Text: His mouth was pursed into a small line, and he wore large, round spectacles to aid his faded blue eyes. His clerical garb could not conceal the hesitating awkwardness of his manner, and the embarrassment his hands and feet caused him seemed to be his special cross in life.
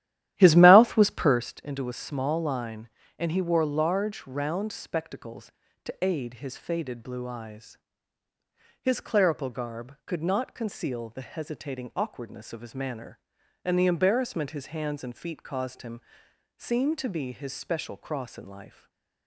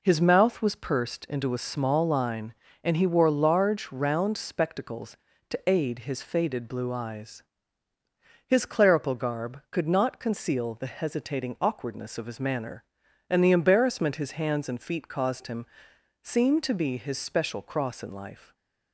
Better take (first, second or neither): second